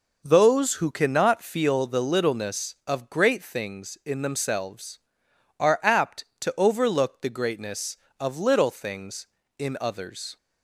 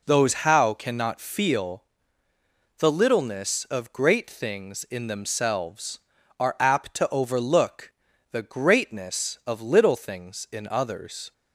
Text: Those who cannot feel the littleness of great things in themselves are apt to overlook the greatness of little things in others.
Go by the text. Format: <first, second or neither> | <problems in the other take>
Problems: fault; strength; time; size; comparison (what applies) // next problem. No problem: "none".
first | says "how" for "who"; at 0.3 s // pauses between "feel" and "the"; noticeable; at 1.8 s; 0.94 s long // pauses between "overlook" and "the"; at 7.9 s; 0.40 s long